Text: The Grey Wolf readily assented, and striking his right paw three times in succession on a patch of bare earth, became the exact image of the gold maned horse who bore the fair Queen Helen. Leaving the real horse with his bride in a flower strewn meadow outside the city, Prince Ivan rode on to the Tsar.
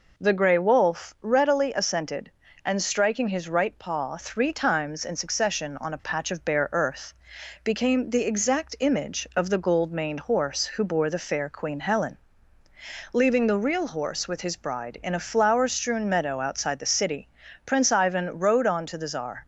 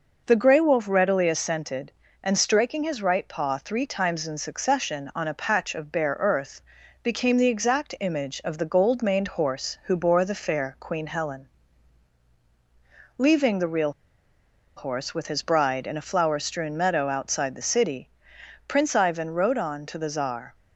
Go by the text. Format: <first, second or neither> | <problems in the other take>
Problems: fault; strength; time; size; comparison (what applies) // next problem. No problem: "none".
first | pauses between "real" and "horse"; noticeable; at 13.9 s; 0.84 s long